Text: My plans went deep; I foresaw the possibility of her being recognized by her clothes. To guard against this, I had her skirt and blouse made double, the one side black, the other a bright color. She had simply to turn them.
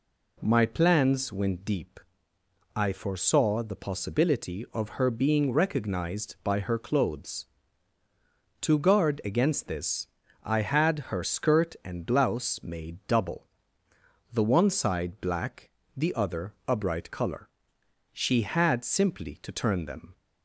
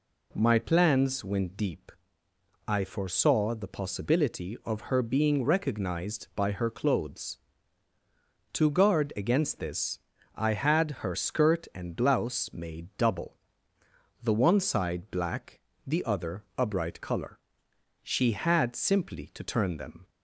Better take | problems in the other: neither | none

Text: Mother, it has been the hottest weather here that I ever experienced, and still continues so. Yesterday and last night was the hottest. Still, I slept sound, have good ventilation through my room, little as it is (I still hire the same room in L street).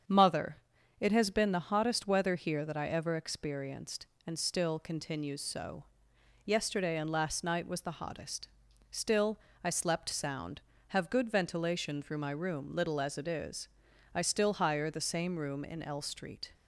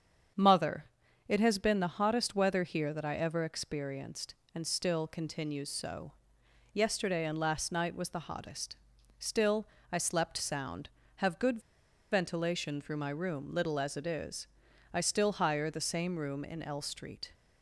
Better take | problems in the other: first | starts louder than the rest; strong; until 1.7 s; 7.5 dB; strong in the first // pauses between "good" and "ventilation"; noticeable; at 11.5 s; 0.52 s long

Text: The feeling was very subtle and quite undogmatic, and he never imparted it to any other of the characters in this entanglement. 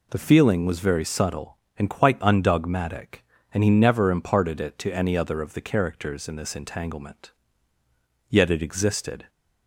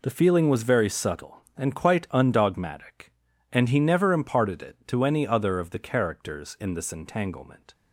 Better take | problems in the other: second | goes on to say "Yet it existed"; noticeable; from 8.2 s on; 1.0 s long

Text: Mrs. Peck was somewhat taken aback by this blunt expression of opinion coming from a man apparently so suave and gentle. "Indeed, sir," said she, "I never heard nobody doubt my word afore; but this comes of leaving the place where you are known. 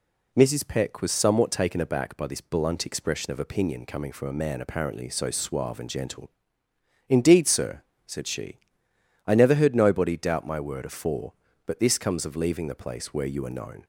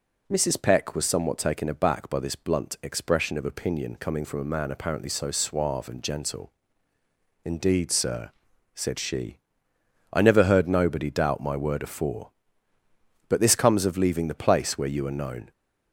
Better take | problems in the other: neither | none

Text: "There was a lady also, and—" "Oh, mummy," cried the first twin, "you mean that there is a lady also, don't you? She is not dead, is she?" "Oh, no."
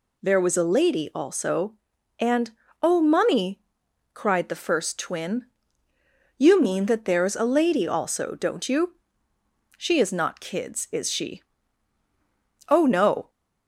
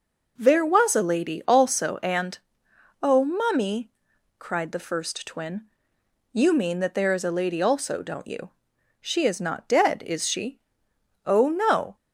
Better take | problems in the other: second | says "kids" for "dead"; at 10.3 s

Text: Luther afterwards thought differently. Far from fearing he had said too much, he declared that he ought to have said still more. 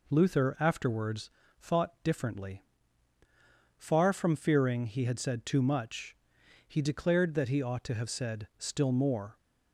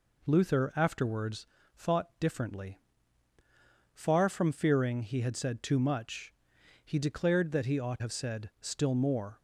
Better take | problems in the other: first | pauses between "afterwards" and "thought"; slight; at 1.4 s; 0.30 s long; slight in the first // skips "to"; at 7.9 s

